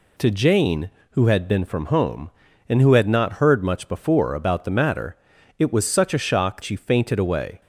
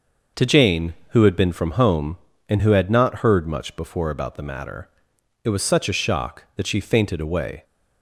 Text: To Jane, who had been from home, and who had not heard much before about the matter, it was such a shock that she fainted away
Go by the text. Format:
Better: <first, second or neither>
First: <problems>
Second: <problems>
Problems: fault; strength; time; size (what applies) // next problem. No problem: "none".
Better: second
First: skips "that"; at 6.6 s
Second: none